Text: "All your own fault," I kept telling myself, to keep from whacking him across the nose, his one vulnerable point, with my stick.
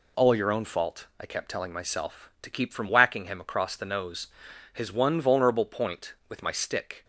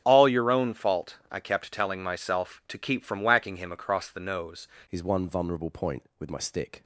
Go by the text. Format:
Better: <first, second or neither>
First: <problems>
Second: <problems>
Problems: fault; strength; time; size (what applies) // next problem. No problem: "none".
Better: first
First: none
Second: starts louder than the rest; strong; until 1.0 s; 8 dB // changes voice at "his"; from 4.8 s on; 2.0 s long